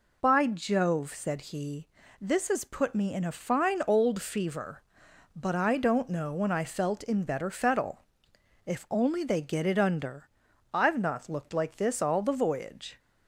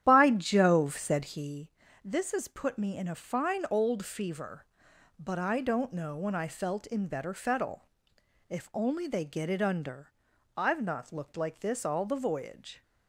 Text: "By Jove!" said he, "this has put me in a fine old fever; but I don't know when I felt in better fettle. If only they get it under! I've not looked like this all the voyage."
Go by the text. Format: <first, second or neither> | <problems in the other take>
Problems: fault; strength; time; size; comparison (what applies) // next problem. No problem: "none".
first | starts louder than the rest; strong; until 1.5 s; 10.5 dB